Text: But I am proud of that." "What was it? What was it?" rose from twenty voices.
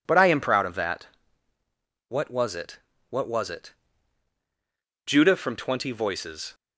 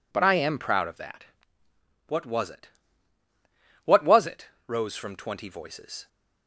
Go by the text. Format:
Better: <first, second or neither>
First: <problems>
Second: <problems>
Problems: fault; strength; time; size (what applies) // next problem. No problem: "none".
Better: second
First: says "judah" for "rose"; at 5.0 s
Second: none